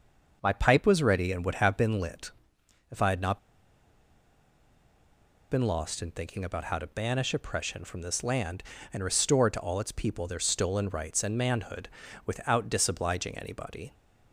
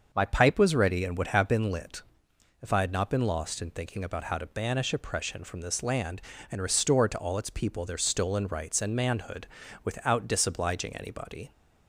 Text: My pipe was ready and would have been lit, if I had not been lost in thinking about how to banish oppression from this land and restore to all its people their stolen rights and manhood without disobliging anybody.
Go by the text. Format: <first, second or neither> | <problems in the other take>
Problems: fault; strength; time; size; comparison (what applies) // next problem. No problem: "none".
second | starts louder than the rest; until 1.4 s; 6 dB; also in the second // pauses between "not" and "been"; strong; at 3.3 s; 2.1 s long // pauses between "manhood" and "without"; at 11.8 s; 0.38 s long; also in the second